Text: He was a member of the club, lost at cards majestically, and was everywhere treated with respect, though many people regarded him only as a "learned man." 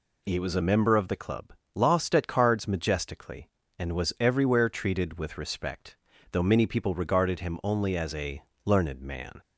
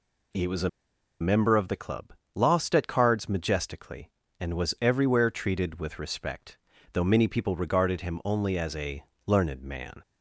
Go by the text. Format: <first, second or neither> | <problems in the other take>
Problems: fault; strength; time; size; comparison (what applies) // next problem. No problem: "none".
first | pauses between "a" and "member"; noticeable; at 0.6 s; 0.51 s long // pauses between "a" and "learned"; slight; at 9.0 s; 0.24 s long; slight in the first